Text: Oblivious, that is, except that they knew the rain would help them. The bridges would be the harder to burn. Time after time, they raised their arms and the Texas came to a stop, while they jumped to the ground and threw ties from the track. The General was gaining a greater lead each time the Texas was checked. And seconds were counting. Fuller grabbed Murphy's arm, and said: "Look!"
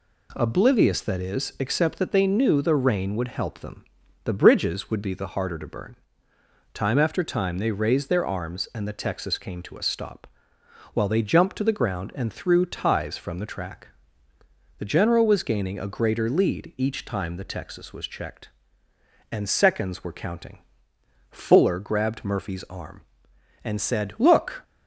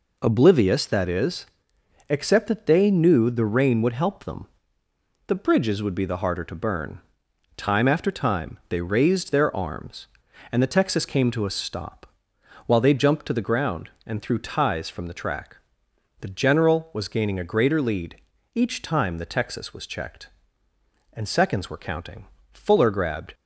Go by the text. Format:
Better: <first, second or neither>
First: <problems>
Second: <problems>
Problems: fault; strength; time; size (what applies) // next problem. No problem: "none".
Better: first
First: none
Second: pauses between "lead" and "each"; at 18.1 s; 0.38 s long // stops before "Murphy's arm and said Look"; at 23.3 s